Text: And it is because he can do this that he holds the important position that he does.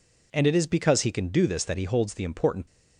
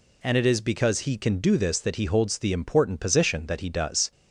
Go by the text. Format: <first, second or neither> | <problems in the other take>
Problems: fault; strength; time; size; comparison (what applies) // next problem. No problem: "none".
second | stops before "position that he does"; at 2.6 s